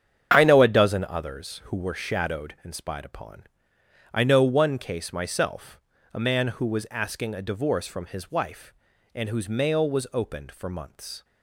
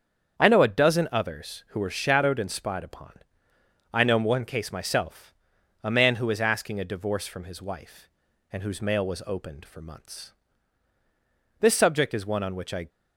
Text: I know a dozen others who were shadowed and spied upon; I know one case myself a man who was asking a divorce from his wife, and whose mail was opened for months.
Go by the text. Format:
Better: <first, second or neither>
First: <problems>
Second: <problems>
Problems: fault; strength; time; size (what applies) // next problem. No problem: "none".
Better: first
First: starts louder than the rest; strong; until 1.3 s; 8.5 dB // pauses between "myself" and "a"; slight; at 5.7 s; 0.36 s long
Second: starts louder than the rest; strong; until 1.4 s; 7.5 dB // pauses between "myself" and "a"; noticeable; at 5.3 s; 0.50 s long // goes on to say "This subject is one on which I"; noticeable; from 11.6 s on; 1.2 s long